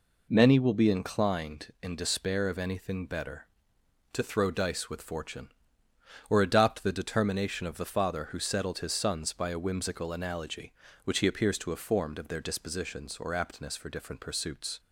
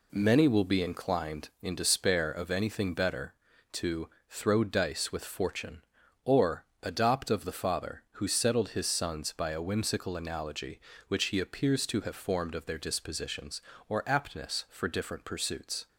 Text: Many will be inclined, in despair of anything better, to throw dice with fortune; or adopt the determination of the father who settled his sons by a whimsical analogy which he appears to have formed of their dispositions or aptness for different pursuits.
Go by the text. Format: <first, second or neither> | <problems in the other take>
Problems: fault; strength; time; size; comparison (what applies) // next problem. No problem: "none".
first | pauses between "to" and "throw"; slight; at 4.0 s; 0.22 s long // pauses between "or" and "adopt"; slight; at 6.6 s; 0.18 s long // skips "the determination"; at 7.2 s